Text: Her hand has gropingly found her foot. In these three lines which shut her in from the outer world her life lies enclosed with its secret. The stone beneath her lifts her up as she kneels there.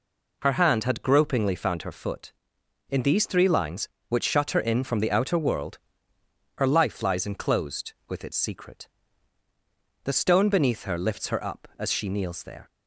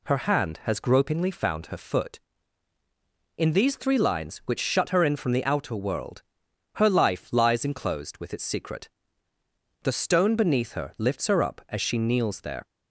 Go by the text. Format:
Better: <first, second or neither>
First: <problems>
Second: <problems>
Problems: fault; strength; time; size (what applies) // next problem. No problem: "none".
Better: second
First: says "had" for "has"; at 0.8 s // pauses between "world" and "her"; noticeable; at 5.7 s; 0.78 s long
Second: pauses between "world" and "her"; noticeable; at 6.2 s; 0.52 s long